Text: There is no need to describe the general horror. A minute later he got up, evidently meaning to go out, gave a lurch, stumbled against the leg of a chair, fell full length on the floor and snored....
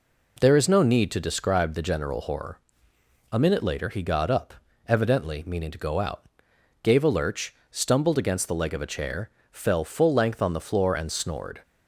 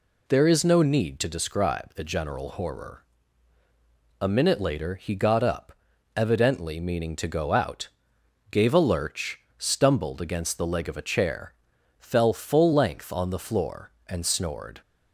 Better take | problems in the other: neither | none

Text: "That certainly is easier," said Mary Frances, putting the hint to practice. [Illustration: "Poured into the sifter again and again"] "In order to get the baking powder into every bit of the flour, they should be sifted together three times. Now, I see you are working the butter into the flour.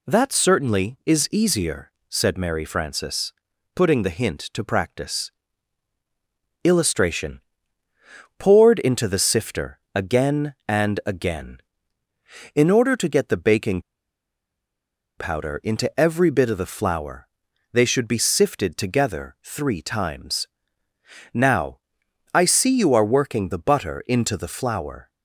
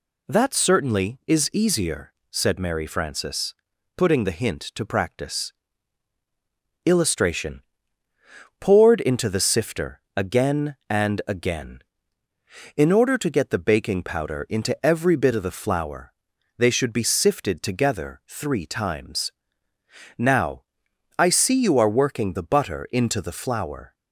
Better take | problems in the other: second | pauses between "sifter" and "again"; slight; at 9.7 s; 0.16 s long; slight in the second // pauses between "baking" and "powder"; strong; at 13.7 s; 1.3 s long

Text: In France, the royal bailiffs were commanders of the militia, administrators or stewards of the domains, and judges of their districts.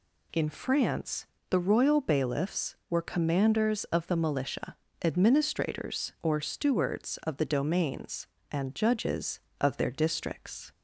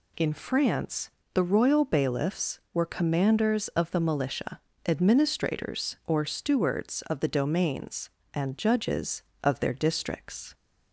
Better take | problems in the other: neither | none

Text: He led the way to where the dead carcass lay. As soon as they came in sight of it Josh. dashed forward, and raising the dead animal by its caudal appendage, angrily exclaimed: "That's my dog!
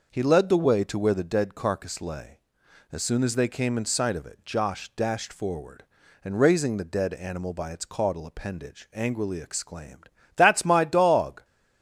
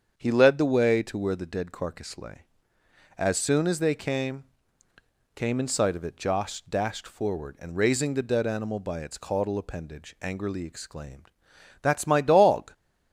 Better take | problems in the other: first | starts louder than the rest; strong; until 1.1 s; 7 dB // says "came" twice; at 5.3 s

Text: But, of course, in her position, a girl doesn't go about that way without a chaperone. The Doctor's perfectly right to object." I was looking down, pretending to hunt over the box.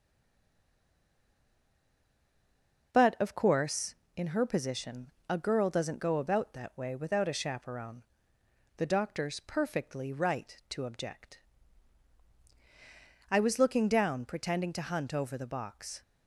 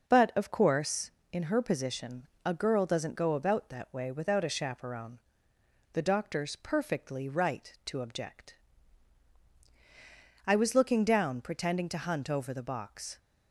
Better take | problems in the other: second | stays silent before the first word; strong; until 2.9 s; 2.9 s long

